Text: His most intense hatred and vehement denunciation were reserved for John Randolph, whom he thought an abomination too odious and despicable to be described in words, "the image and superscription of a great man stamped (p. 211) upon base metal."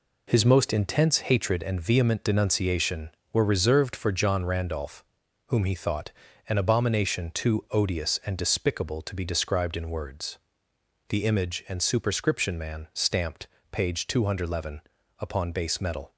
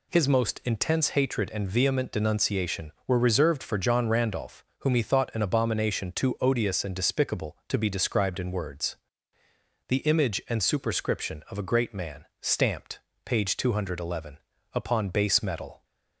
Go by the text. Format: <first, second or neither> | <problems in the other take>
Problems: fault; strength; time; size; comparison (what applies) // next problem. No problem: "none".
second | pauses between "thought" and "an"; slight; at 6.1 s; 0.36 s long // skips "of a great"; at 12.5 s